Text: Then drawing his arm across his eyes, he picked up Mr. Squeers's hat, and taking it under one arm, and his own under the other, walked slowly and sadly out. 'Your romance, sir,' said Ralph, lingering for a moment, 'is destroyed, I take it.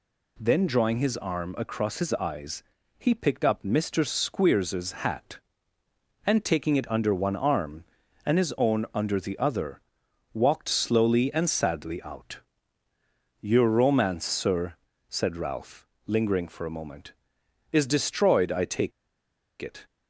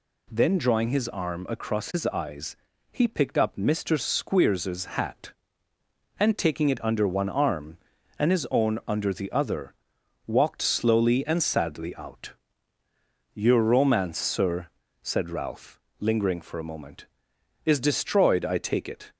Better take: second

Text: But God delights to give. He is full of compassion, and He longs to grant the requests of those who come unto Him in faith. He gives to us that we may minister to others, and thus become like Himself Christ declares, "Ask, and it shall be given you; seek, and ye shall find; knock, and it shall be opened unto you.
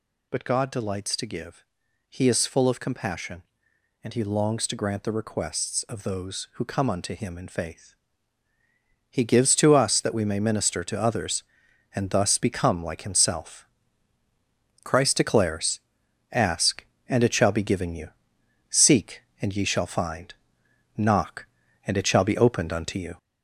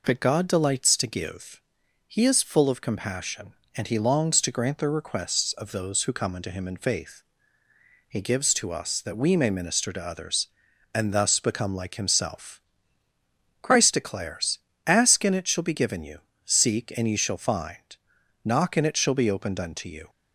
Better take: second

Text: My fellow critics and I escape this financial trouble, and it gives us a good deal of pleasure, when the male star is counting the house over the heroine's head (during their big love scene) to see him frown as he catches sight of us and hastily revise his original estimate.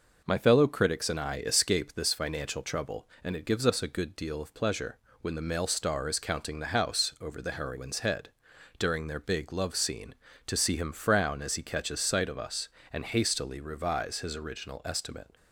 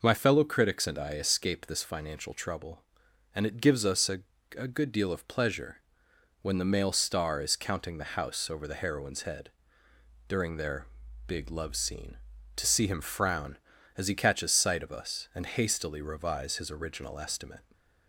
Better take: first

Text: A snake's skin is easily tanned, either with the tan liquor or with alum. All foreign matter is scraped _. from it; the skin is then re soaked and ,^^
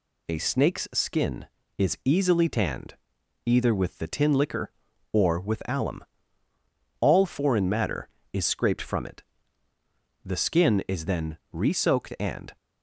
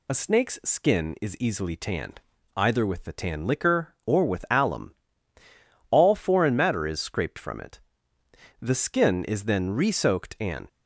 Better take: second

